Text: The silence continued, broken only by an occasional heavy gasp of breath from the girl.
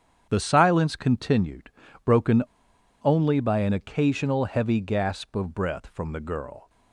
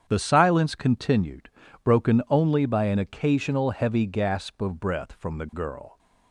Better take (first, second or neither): second